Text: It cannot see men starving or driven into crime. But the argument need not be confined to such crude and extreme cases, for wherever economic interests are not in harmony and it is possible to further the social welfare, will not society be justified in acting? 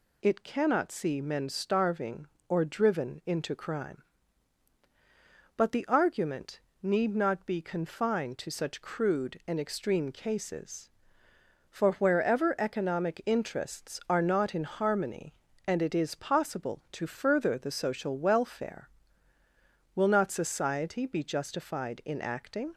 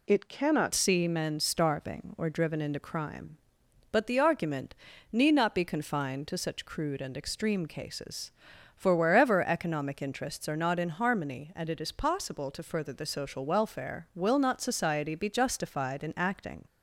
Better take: first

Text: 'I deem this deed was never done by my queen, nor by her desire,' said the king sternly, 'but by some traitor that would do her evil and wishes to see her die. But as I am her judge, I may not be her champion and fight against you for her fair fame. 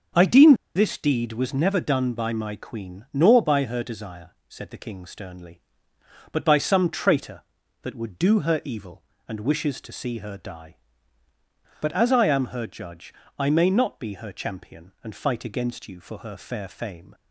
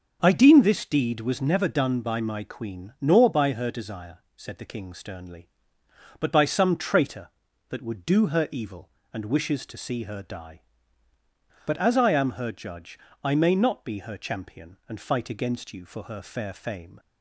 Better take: second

